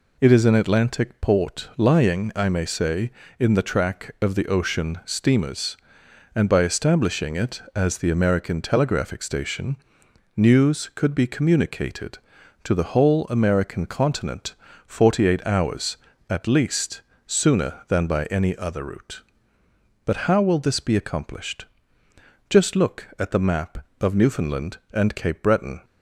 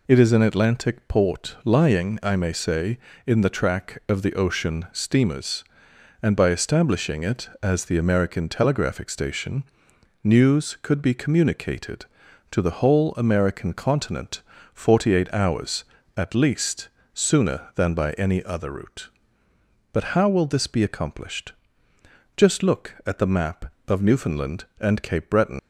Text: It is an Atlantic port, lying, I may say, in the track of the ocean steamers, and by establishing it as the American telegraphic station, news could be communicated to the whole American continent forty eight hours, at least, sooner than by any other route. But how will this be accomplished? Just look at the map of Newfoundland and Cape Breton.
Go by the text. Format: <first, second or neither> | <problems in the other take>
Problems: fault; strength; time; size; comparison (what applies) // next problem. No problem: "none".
first | pauses between "continent" and "forty"; slight; at 14.4 s; 0.32 s long; slight in the first // leaves "Breton" unfinished; at 25.5 s; 120 ms